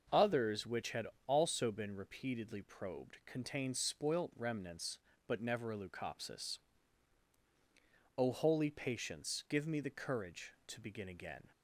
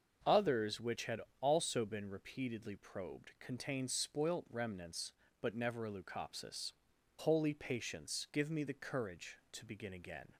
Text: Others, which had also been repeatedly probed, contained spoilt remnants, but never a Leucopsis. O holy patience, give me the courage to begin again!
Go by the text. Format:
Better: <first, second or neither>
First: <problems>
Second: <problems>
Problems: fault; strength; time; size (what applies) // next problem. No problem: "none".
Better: first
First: starts louder than the rest; noticeable; until 1.3 s; 6 dB // pauses between "had" and "also"; slight; at 1.0 s; 0.20 s long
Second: starts louder than the rest; until 1.4 s; 6.5 dB // pauses between "had" and "also"; slight; at 1.2 s; 0.20 s long // skips "O"; at 6.9 s